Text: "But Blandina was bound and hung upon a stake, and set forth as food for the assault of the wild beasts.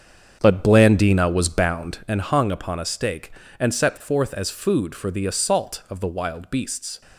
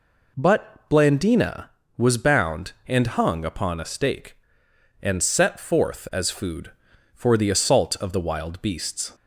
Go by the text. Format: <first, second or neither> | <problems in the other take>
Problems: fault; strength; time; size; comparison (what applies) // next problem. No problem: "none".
second | starts louder than the rest; strong; until 2.0 s; 7.5 dB